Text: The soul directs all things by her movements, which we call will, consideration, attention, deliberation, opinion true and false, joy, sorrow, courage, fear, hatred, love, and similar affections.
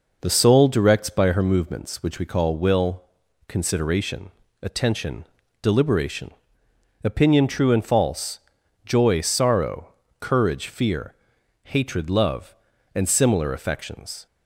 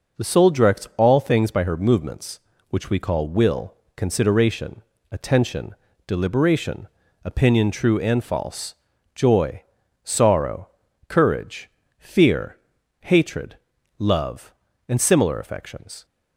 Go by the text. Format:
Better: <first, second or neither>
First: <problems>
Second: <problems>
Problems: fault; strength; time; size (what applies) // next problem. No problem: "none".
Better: second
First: skips "all things"; at 1.0 s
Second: none